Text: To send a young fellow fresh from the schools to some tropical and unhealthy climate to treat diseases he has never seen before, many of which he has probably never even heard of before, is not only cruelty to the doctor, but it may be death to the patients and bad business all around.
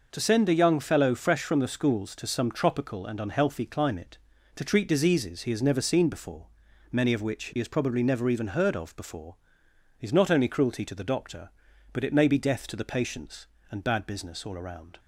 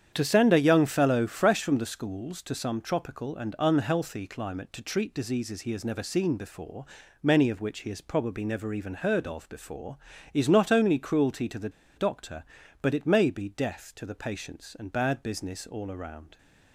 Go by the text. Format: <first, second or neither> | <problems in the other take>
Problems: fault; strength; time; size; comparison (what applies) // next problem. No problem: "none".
first | starts louder than the rest; strong; until 1.1 s; 8.5 dB // pauses between "the" and "doctor"; slight; at 11.7 s; 0.26 s long